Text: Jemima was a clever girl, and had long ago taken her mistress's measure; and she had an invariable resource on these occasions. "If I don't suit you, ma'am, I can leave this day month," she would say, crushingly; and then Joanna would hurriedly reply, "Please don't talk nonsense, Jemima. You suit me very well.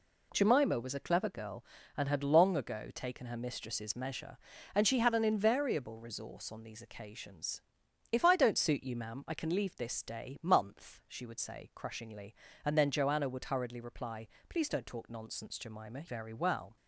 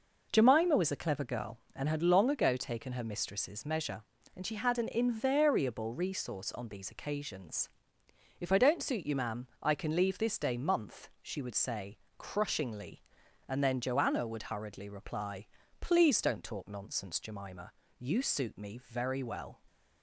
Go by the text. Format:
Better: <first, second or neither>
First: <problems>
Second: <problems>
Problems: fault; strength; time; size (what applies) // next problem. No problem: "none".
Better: second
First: skips "You suit me"; at 16.0 s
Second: none